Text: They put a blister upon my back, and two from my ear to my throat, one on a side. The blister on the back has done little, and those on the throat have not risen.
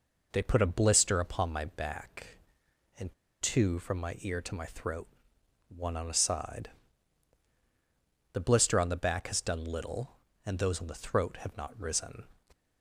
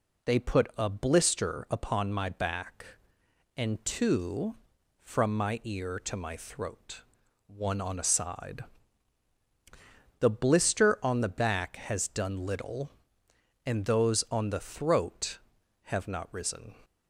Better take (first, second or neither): second